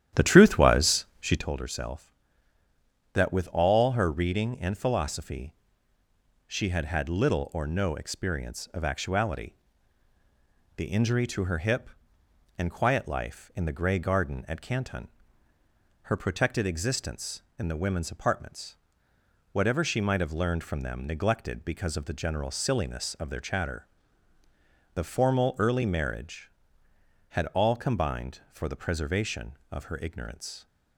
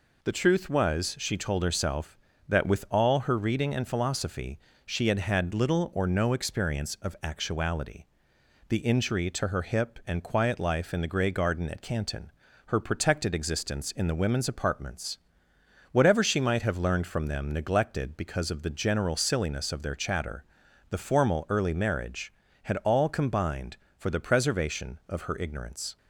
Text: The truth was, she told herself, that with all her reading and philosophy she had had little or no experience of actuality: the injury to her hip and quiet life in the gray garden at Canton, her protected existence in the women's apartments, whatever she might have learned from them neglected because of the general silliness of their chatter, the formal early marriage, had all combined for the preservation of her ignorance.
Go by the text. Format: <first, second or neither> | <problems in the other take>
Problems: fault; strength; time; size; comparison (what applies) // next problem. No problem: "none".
second | starts louder than the rest; strong; until 1.5 s; 11 dB // pauses between "philosophy" and "she"; noticeable; at 5.5 s; 0.92 s long; slight in the second